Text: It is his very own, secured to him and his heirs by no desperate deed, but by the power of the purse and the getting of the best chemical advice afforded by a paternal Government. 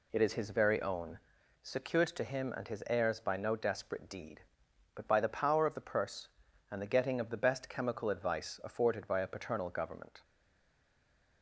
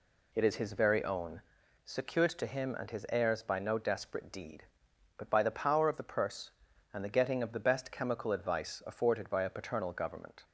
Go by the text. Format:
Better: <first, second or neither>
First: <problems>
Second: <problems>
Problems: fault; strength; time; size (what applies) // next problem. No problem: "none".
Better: second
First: stays silent after the last word; noticeable; from 10.2 s on; 1.2 s long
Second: none